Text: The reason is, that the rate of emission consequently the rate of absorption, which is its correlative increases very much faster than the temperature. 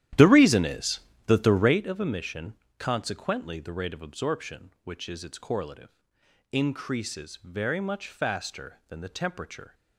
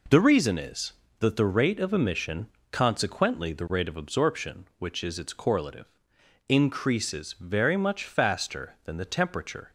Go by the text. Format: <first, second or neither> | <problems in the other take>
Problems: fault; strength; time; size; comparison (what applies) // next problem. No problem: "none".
second | starts louder than the rest; strong; until 1.9 s; 12 dB // pauses between "emission" and "consequently"; slight; at 2.5 s; 0.24 s long; slight in the second // pauses between "correlative" and "increases"; noticeable; at 5.8 s; 0.62 s long; noticeable in the second